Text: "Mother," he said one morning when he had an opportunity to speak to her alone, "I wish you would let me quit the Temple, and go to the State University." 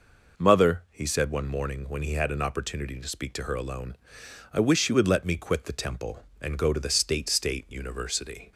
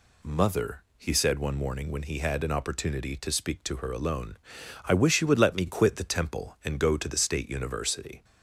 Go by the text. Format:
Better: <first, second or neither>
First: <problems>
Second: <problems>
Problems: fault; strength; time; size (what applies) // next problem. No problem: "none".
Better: second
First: says "State" twice; at 7.2 s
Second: none